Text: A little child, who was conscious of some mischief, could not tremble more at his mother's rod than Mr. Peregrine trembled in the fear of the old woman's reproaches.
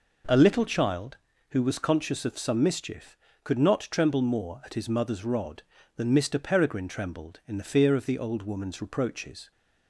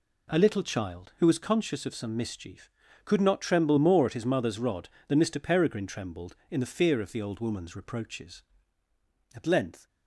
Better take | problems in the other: first | goes on to say "At length"; from 9.3 s on; 0.54 s long

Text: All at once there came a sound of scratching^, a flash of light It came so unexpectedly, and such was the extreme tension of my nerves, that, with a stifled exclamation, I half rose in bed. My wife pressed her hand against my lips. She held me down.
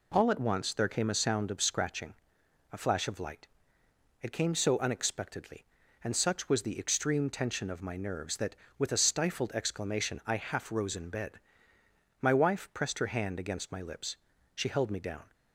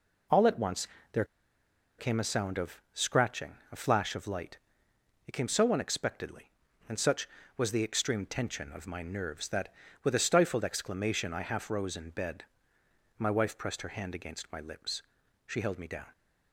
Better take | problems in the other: first | pauses between "once" and "there"; slight; at 0.8 s; 0.26 s long // pauses between "there" and "came"; noticeable; at 1.2 s; 0.74 s long // pauses between "light" and "It"; noticeable; at 4.5 s; 0.68 s long; noticeable in the first

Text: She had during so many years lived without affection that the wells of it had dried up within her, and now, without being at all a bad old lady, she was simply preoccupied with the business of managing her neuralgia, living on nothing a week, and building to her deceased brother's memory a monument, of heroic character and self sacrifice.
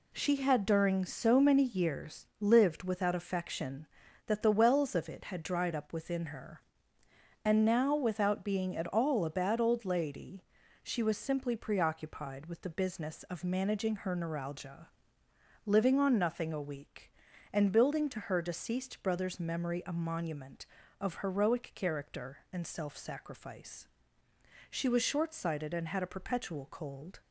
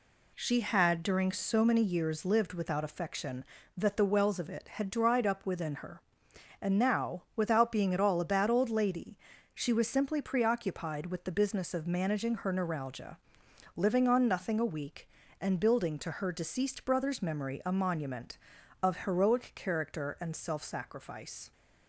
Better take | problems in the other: second | goes on to say "She was short sighted and had a perpetual cold"; strong; from 24.6 s on; 2.5 s long

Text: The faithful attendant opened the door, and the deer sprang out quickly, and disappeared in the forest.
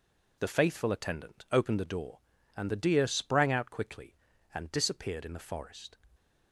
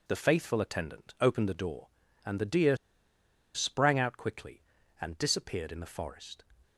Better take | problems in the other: first | pauses between "deer" and "sprang"; noticeable; at 2.7 s; 0.77 s long

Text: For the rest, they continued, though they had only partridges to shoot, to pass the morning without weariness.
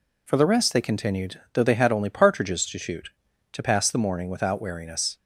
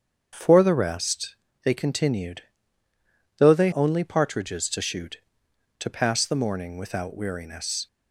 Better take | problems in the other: first | starts louder than the rest; strong; until 1.3 s; 7 dB // skips "had"; at 3.7 s

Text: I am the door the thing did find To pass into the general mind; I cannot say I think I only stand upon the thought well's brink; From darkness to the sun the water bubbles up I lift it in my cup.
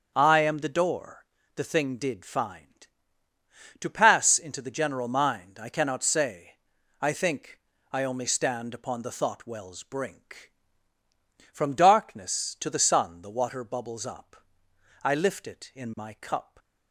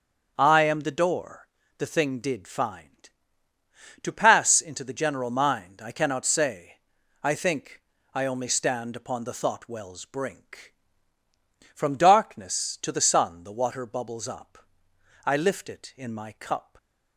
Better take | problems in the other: neither | starts louder than the rest; the same in both // pauses between "door" and "the"; slight; the same in both // pauses between "say" and "I"; the same in both // pauses between "think" and "I"; slight; the same in both // pauses between "up" and "I"; noticeable; the same in both

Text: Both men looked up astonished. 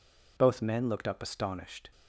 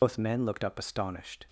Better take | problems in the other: first | loses the start of "Both"; at 0.0 s; 70 ms

